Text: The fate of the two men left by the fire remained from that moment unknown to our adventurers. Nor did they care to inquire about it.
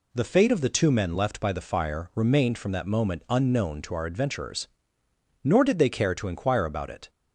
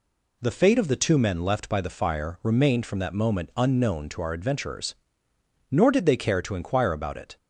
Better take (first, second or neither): neither